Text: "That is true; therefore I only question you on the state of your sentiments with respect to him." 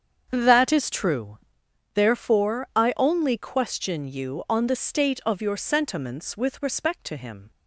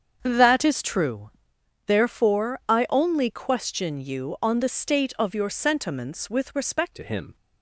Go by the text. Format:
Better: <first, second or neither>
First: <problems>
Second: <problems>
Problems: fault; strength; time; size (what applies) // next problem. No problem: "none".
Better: first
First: starts louder than the rest; strong; until 1.3 s; 7.5 dB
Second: starts louder than the rest; strong; until 1.2 s; 7 dB // changes voice at "to"; from 6.9 s on; 0.4 s long